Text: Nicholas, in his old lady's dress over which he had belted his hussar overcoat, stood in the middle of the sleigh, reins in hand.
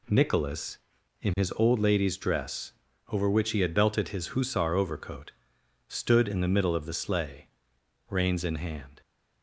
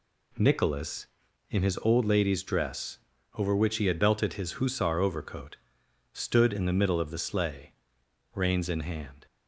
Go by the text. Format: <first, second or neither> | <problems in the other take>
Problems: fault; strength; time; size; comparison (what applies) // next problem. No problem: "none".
neither | pauses between "dress" and "over"; the same in both